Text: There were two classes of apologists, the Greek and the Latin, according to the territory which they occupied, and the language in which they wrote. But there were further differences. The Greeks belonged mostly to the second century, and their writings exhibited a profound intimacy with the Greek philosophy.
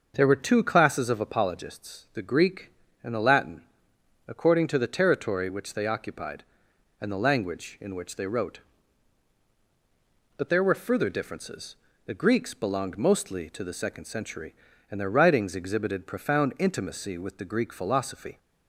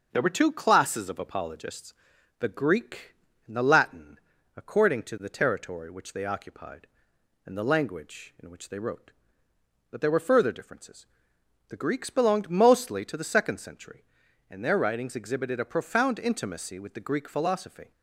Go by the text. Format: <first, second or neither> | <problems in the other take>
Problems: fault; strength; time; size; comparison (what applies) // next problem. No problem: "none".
second | starts louder than the rest; noticeable; until 1.1 s; 6 dB; also in the second // skips "a"; at 16.0 s